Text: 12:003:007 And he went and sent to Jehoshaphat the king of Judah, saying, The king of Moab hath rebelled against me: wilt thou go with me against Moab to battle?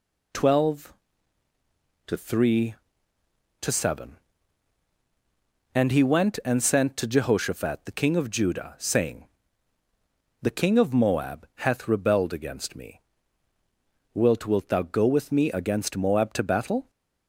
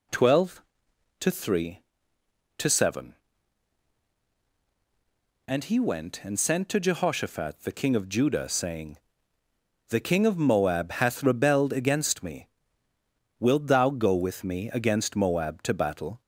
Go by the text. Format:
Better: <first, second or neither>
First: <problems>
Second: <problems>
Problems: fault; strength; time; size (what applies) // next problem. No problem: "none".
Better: second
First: says "wilt" twice; at 14.4 s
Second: none